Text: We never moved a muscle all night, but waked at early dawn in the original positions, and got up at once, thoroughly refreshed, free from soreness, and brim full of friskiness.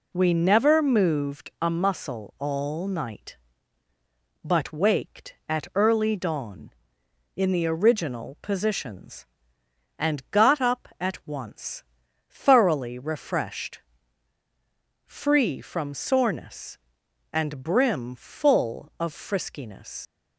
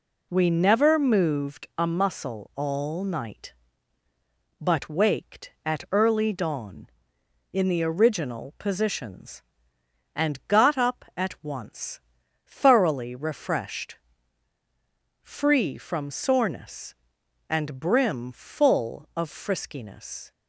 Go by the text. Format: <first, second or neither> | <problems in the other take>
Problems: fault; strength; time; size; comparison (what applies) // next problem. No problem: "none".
second | leaves "friskiness" unfinished; at 20.0 s; 90 ms